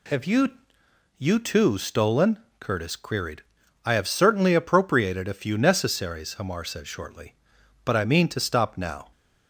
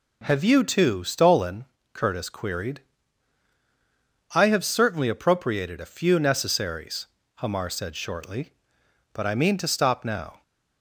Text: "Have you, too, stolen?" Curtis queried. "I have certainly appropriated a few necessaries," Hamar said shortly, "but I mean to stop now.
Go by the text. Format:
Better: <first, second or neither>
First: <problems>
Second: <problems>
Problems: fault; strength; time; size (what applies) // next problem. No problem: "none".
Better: second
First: says "you" twice; at 1.1 s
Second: none